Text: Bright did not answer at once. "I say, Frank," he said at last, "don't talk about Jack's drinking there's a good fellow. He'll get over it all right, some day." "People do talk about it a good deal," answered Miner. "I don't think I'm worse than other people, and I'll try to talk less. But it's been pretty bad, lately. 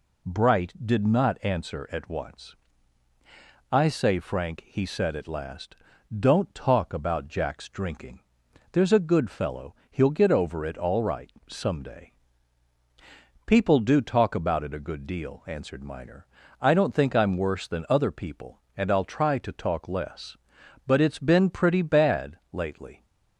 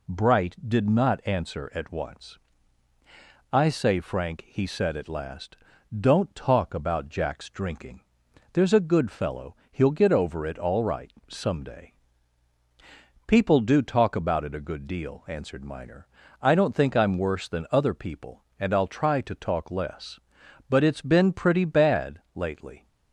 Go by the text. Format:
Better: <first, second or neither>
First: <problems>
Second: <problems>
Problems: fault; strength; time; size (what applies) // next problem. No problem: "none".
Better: neither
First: pauses between "drinking" and "there's"; noticeable; at 8.1 s; 0.54 s long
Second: pauses between "drinking" and "there's"; noticeable; at 7.9 s; 0.54 s long